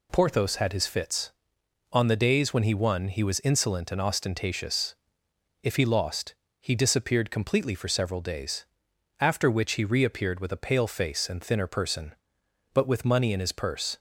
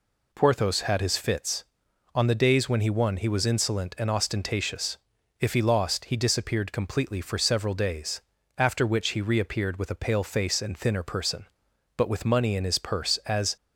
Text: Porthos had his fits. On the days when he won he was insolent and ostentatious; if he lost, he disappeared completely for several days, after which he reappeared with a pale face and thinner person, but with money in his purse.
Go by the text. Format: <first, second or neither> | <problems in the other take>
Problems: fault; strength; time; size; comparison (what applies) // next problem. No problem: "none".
first | goes on to say "As"; slight; from 13.2 s on; 0.30 s long